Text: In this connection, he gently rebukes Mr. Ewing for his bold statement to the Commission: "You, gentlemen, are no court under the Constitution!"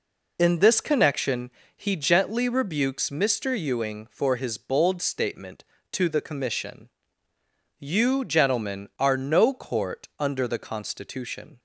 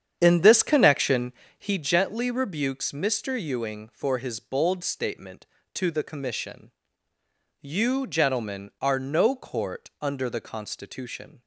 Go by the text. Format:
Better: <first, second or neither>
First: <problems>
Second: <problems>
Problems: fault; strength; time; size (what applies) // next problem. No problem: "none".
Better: first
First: none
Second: starts louder than the rest; strong; until 1.8 s; 8.5 dB